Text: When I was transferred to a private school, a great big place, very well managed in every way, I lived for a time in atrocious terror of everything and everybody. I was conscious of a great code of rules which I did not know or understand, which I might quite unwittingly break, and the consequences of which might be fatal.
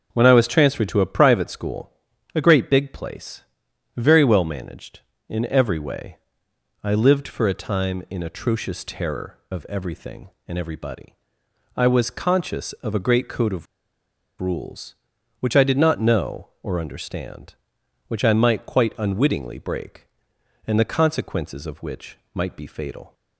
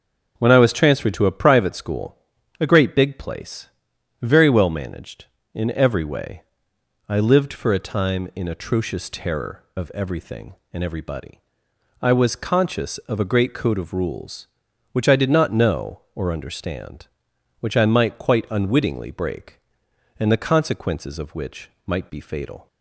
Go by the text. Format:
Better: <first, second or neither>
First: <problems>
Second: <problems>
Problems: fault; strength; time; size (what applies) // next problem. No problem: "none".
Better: second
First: starts louder than the rest; until 1.1 s; 6 dB // pauses between "of" and "rules"; noticeable; at 13.6 s; 0.75 s long // pauses between "which" and "might"; slight; at 22.1 s; 0.16 s long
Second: starts louder than the rest; until 1.3 s; 6 dB // pauses between "which" and "might"; slight; at 21.6 s; 0.16 s long